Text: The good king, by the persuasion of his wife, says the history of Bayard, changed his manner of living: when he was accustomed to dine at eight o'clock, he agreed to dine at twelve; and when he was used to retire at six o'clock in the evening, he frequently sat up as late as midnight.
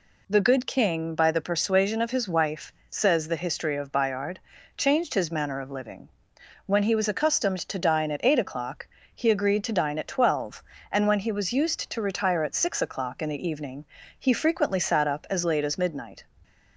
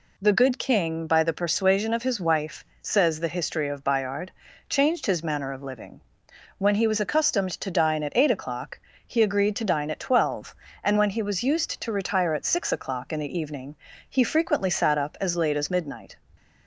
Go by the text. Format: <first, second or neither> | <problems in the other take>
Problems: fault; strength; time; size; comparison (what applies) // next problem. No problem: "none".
neither | none